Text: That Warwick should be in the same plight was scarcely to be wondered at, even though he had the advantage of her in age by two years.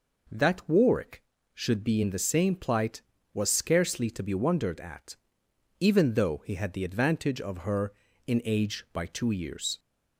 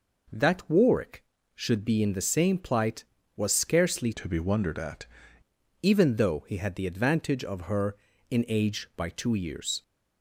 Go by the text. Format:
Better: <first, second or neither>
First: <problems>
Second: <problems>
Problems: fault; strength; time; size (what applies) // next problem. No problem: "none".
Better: first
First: none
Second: changes voice from "to" to "at"; from 4.1 to 5.0 s; 0.9 s long